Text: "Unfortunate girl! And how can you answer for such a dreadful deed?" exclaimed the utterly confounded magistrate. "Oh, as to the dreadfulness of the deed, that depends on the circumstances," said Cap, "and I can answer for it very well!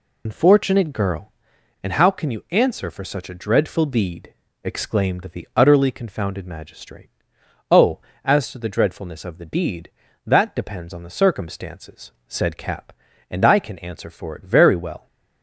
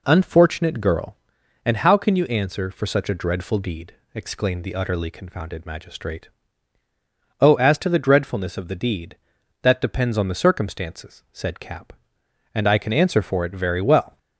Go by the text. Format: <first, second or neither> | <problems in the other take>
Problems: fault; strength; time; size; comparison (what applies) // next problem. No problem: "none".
second | loses the start of "Unfortunate"; at 0.2 s; 55 ms